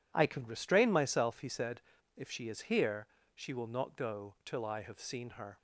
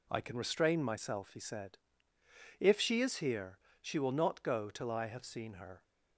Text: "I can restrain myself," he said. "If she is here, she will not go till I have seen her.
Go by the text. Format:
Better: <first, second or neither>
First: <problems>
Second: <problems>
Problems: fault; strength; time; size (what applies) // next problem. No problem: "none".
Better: neither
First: none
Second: none